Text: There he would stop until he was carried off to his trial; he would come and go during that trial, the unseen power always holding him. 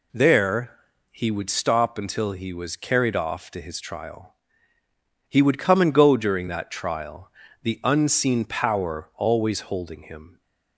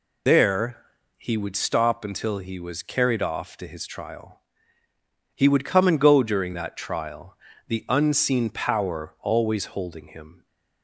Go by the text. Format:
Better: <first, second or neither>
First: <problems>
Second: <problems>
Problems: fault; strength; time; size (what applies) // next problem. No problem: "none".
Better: first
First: pauses between "There" and "he"; slight; at 0.7 s; 0.36 s long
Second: loses the start of "There"; at 0.2 s; 75 ms // pauses between "There" and "he"; slight; at 0.8 s; 0.36 s long